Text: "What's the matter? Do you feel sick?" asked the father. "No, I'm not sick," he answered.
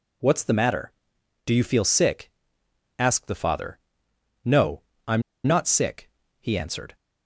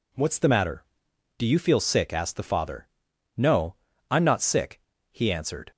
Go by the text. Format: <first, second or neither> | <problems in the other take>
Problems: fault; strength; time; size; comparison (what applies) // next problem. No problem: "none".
second | pauses between "I'm" and "not"; slight; at 5.2 s; 0.25 s long